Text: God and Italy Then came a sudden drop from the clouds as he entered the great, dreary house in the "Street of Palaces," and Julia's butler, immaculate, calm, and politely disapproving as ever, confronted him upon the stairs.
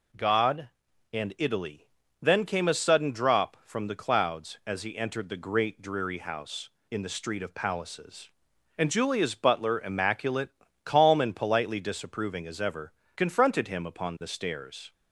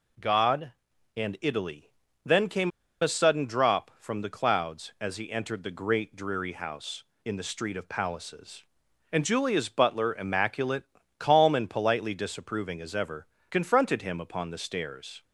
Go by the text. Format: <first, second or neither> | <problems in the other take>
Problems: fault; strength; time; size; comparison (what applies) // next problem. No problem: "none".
first | pauses between "Italy" and "Then"; slight; at 1.9 s; 0.34 s long; slight in the first // pauses between "came" and "a"; slight; at 2.7 s; 0.31 s long